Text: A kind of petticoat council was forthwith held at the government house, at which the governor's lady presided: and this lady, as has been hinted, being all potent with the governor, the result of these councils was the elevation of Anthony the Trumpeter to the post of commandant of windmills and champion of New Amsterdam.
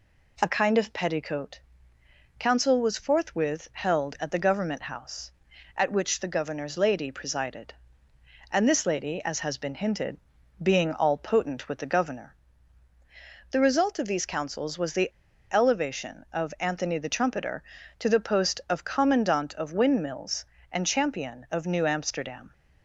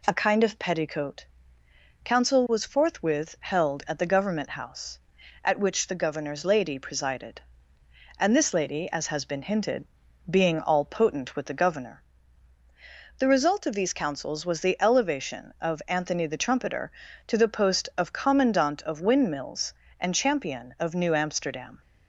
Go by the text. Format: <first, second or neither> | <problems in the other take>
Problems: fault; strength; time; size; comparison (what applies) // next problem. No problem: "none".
second | pauses between "petticoat" and "council"; noticeable; at 1.6 s; 0.78 s long; noticeable in the second // pauses between "the" and "elevation"; at 15.0 s; 0.43 s long